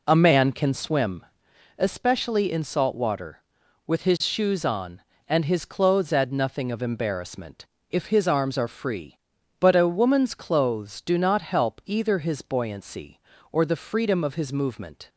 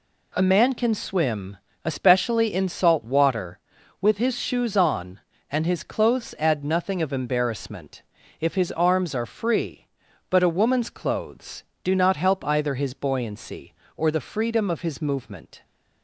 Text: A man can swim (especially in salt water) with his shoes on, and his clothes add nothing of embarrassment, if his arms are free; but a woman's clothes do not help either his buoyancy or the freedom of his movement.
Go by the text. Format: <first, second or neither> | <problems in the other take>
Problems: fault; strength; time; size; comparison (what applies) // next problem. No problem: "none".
second | starts louder than the rest; until 1.7 s; 4 dB